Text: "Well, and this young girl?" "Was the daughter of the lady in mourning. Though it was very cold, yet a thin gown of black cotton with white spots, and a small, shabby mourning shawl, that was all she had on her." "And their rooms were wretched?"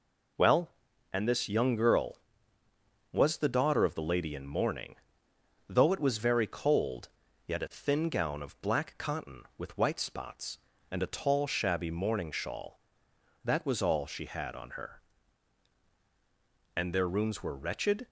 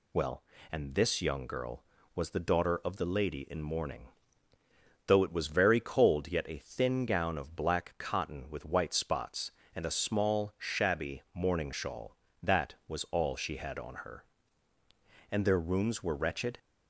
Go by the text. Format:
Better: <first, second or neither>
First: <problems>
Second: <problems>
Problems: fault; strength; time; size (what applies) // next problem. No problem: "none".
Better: second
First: says "tall" for "small"; at 11.1 s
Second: none